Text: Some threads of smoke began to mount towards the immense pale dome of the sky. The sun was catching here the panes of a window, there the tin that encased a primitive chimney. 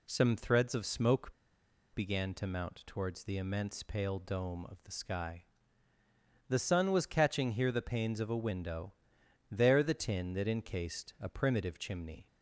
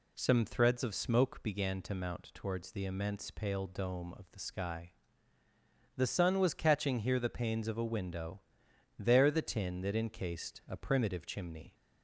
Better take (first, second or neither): second